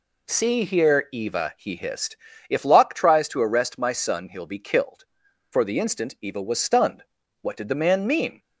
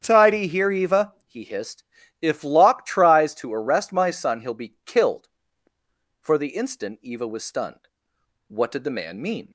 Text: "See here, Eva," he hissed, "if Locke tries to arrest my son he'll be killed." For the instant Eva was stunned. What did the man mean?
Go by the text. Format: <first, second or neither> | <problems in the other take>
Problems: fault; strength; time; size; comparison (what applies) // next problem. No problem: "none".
first | starts louder than the rest; strong; until 1.0 s; 8 dB // says "Tidy" for "See"; at 0.0 s